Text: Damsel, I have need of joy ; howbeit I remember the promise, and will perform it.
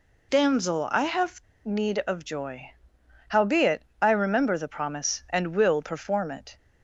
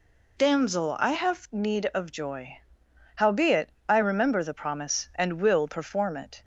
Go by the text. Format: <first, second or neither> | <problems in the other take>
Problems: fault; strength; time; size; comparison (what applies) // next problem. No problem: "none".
second | pauses between "have" and "need"; slight; at 1.4 s; 0.23 s long // pauses between "howbeit" and "I"; slight; at 3.8 s; 0.18 s long; slight in the second